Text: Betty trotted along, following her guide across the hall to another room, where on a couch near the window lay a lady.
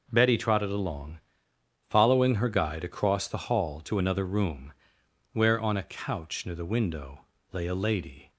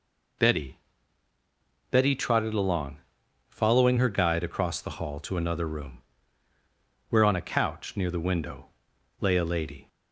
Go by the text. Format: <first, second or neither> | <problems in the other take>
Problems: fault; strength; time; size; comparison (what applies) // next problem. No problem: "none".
first | says "Betty" twice; at 1.9 s // pauses between "window" and "lay"; noticeable; at 8.6 s; 0.52 s long; slight in the first